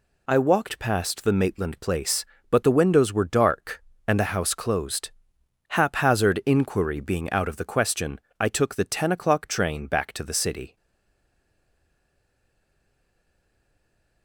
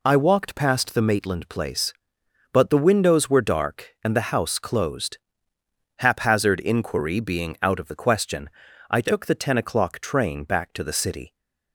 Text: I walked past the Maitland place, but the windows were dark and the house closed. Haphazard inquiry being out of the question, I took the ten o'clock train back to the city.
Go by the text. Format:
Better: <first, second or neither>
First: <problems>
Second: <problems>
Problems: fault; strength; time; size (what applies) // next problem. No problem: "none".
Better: second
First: stays silent after the last word; strong; from 10.7 s on; 3.5 s long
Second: none